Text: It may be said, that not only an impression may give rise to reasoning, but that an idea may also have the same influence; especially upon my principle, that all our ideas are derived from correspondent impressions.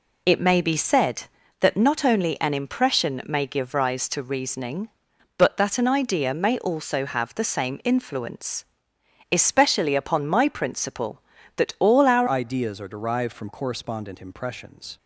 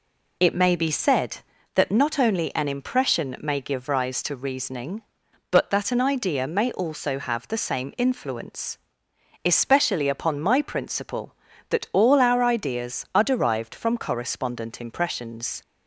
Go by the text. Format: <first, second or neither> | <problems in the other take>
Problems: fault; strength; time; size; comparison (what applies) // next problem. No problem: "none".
second | changes voice at "ideas"; from 12.2 s on; 2.7 s long